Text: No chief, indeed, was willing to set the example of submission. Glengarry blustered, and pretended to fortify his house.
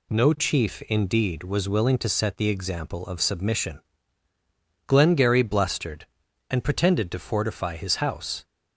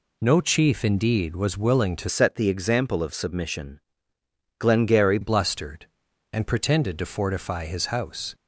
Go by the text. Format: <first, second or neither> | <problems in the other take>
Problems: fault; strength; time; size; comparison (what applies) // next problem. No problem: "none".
first | changes voice from "set" to "Glengarry"; from 2.0 to 5.1 s; 3.1 s long